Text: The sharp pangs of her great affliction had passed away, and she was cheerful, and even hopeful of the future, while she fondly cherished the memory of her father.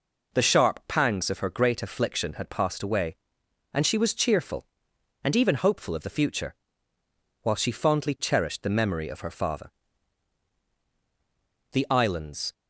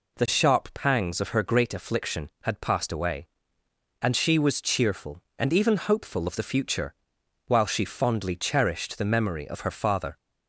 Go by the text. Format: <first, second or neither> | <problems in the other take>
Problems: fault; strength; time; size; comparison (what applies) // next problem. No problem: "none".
second | goes on to say "The islands"; noticeable; from 11.7 s on; 0.80 s long